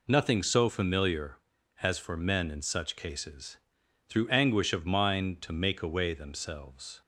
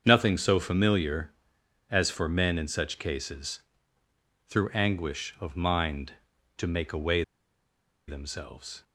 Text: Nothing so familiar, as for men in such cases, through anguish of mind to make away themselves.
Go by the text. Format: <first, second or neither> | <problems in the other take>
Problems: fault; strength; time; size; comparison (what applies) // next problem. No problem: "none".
first | starts louder than the rest; until 1.0 s; 7 dB // pauses between "away" and "themselves"; noticeable; at 7.2 s; 0.85 s long